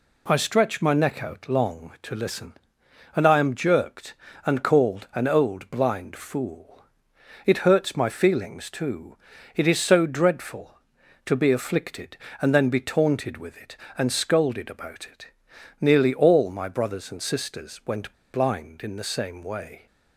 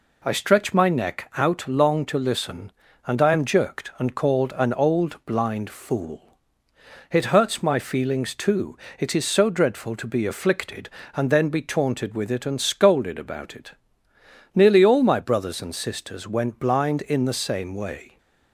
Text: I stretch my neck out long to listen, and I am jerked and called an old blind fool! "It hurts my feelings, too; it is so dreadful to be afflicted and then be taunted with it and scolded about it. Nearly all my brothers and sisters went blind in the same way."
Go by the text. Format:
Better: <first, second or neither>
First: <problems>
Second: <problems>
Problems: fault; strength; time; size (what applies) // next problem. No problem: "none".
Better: second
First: pauses between "went" and "blind"; slight; at 18.1 s; 0.19 s long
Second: none